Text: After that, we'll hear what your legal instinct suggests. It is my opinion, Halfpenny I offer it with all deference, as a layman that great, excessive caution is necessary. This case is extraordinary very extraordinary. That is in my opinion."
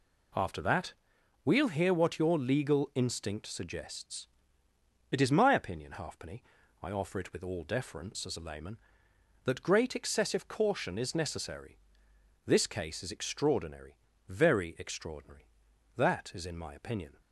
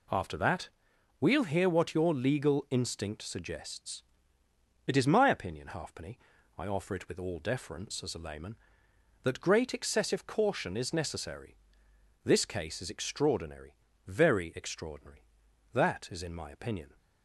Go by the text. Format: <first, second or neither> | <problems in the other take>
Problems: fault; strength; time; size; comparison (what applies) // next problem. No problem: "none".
neither | pauses between "Halfpenny" and "I"; the same in both // pauses between "extraordinary" and "very"; slight; the same in both